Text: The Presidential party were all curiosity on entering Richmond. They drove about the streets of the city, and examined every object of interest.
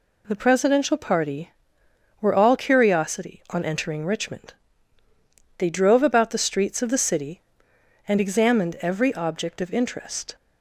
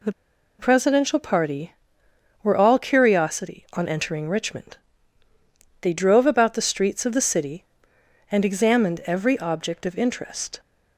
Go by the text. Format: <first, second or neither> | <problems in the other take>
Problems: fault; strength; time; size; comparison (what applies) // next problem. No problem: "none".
first | pauses between "The" and "Presidential"; noticeable; at 0.1 s; 0.46 s long